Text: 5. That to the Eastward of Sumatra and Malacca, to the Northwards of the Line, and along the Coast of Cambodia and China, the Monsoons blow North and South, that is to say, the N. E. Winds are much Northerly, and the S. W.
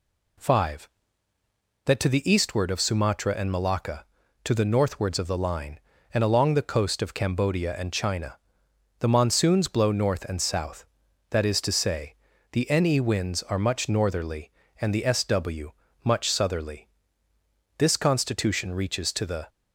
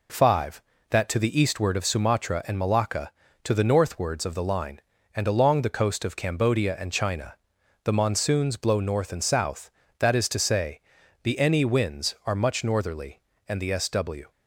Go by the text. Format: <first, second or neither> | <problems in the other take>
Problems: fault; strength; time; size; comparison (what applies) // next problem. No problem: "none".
second | goes on to say "much Southerly This Constitution reaches to the"; strong; from 16.0 s on; 3.4 s long